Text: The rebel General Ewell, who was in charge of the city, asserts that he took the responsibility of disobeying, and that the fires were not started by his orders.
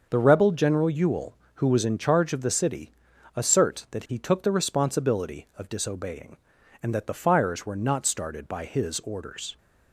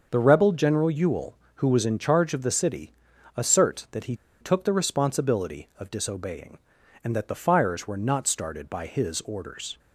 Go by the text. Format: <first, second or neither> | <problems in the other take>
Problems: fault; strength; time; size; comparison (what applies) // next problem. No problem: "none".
first | starts louder than the rest; until 1.1 s; 6.5 dB; also in the first // pauses between "he" and "took"; slight; at 4.1 s; 0.26 s long